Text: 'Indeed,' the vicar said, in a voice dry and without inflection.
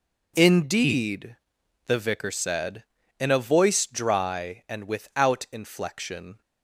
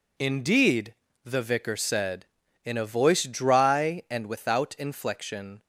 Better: neither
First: none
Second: none

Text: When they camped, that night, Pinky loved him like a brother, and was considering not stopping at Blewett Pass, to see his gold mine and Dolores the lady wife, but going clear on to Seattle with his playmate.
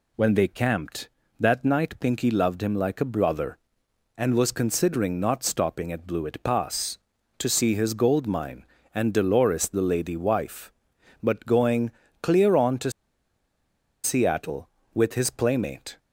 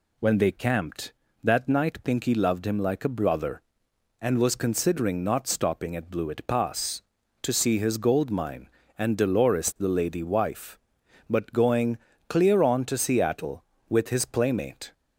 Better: second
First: pauses between "going" and "clear"; slight; at 11.9 s; 0.32 s long // pauses between "to" and "Seattle"; at 12.9 s; 1.1 s long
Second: pauses between "going" and "clear"; slight; at 11.9 s; 0.32 s long

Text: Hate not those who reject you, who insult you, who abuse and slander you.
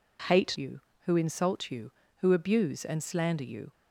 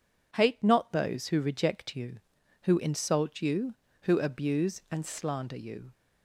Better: second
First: skips "not those who reject"; at 0.5 s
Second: none

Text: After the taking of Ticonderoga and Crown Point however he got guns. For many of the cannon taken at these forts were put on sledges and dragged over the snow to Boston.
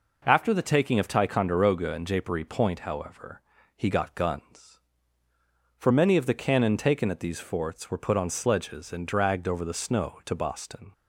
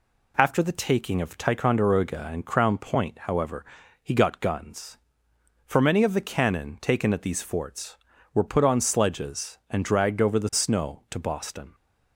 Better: second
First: says "Japery" for "Crown"; at 2.0 s // pauses between "however" and "he"; slight; at 3.4 s; 0.34 s long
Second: pauses between "however" and "he"; at 3.6 s; 0.40 s long

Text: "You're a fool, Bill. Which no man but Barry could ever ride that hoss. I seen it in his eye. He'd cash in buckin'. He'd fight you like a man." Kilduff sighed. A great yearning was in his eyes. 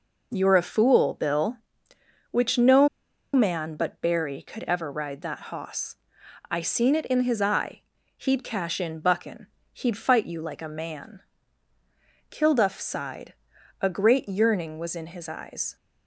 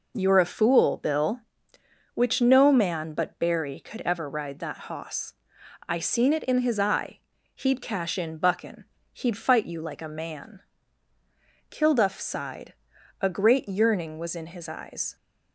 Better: second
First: pauses between "no" and "man"; at 2.8 s; 0.45 s long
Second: none

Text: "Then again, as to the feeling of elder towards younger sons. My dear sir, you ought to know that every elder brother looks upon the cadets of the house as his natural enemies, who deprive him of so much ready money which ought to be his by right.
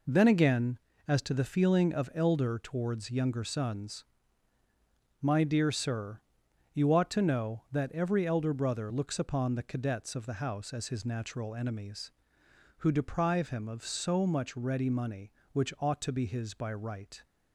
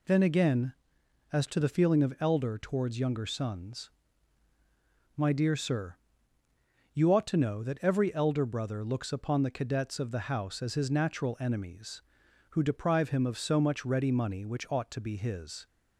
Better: first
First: none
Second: stops before "by right"; at 15.6 s

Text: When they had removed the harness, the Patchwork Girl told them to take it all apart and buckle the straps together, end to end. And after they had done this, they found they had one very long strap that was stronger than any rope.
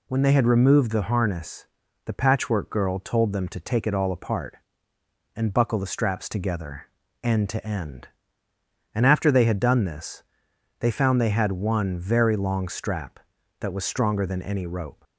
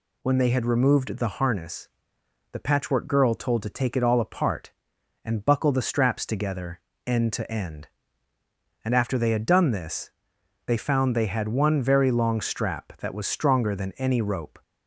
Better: first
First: none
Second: skips "them"; at 3.6 s

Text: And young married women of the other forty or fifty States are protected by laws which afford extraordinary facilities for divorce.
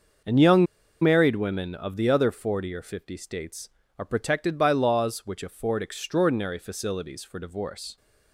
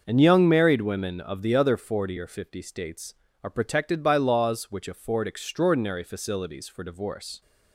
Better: second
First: starts louder than the rest; until 1.6 s; 6 dB // pauses between "young" and "married"; at 0.6 s; 0.36 s long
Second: starts louder than the rest; until 1.0 s; 6.5 dB

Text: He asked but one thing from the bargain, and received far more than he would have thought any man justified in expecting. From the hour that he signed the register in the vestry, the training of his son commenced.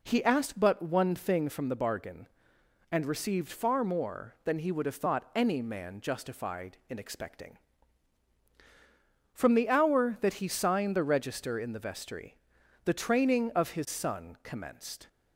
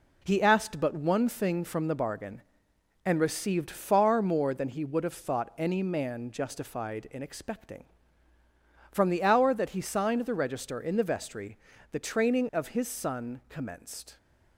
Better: first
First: none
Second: gets quieter; throughout; 6 dB

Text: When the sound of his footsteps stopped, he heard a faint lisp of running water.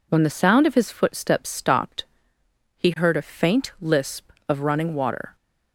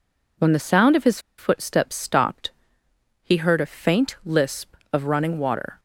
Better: first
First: none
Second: pauses between "his" and "footsteps"; slight; at 1.1 s; 0.19 s long

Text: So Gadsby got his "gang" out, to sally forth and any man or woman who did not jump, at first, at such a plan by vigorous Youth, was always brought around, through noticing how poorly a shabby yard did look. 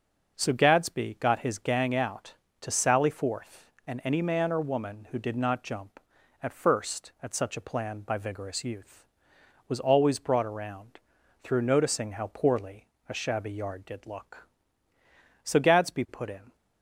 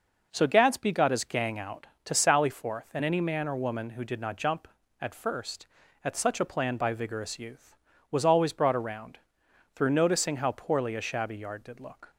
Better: second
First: starts louder than the rest; until 1.4 s; 6 dB // pauses between "poorly" and "a"; slight; at 12.8 s; 0.24 s long // goes on to say "So Gadsby put in"; noticeable; from 15.4 s on; 1.1 s long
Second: none

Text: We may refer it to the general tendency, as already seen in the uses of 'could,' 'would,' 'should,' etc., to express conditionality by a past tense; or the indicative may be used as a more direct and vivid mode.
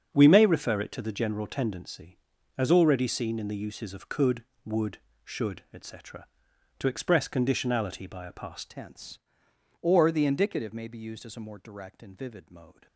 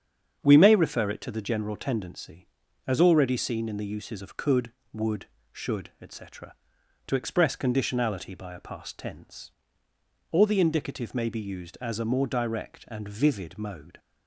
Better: second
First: starts louder than the rest; strong; until 1.1 s; 7 dB // changes voice at "tense"; from 8.6 s on; 4.2 s long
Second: starts louder than the rest; strong; until 1.4 s; 7.5 dB

